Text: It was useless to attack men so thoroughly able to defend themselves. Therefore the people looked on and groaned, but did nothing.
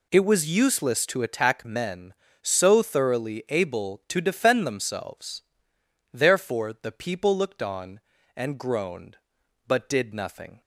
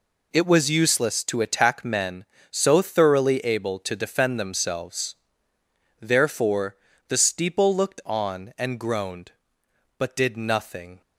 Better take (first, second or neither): first